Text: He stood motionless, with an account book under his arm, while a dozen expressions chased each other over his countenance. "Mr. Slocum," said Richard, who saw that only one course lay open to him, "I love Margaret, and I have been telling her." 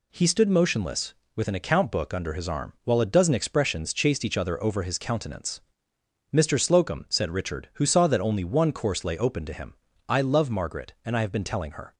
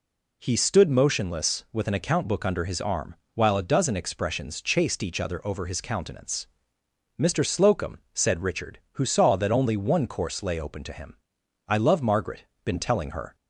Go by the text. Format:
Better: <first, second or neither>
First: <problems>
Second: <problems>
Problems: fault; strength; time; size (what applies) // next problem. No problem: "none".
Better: first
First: none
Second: skips "and I have"; at 12.5 s